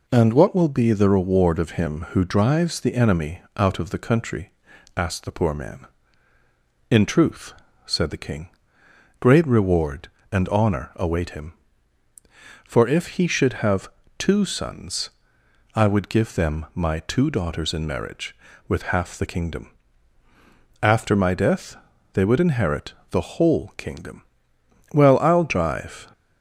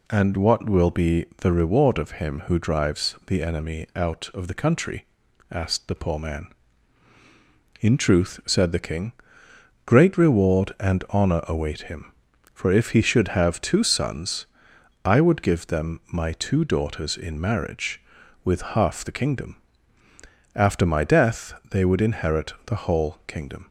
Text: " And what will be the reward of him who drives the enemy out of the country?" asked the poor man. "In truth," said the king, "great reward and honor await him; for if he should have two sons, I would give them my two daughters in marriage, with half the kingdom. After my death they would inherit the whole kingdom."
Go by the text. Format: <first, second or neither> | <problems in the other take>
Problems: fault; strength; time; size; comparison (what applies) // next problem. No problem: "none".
second | pauses between "enemy" and "out"; slight; at 3.4 s; 0.16 s long // pauses between "have" and "two"; slight; at 13.8 s; 0.28 s long // pauses between "death" and "they"; at 21.7 s; 0.38 s long; slight in the second // pauses between "inherit" and "the"; slight; at 22.9 s; 0.16 s long // goes on to say "Well I'll drive"; noticeable; from 24.9 s on; 1.1 s long